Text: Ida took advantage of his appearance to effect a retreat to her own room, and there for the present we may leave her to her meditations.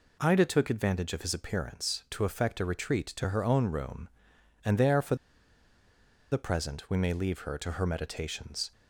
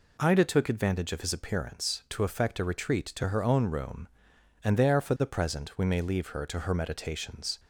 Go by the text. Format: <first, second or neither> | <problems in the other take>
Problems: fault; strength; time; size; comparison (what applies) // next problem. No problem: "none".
second | pauses between "for" and "the"; at 5.1 s; 1.1 s long